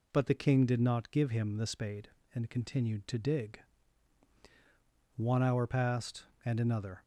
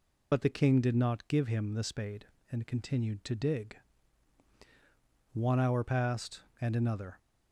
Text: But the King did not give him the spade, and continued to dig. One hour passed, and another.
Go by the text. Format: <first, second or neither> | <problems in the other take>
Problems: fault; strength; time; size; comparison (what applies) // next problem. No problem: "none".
first | loses the start of "But"; at 0.3 s; 45 ms